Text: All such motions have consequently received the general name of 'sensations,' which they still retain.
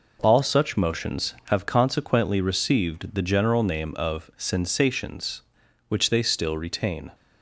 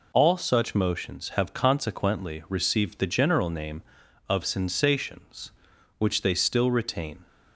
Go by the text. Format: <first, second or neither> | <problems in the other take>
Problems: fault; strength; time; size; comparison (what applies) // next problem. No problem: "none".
neither | none